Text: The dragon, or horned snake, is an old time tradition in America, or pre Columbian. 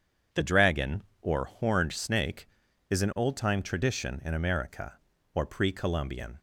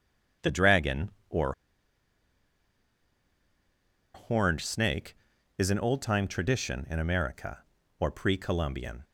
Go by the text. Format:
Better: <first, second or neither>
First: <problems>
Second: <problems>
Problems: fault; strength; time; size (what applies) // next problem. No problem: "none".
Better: first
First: starts louder than the rest; strong; until 1.5 s; 8 dB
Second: starts louder than the rest; strong; until 4.2 s; 8 dB // pauses between "or" and "horned"; strong; at 1.5 s; 2.6 s long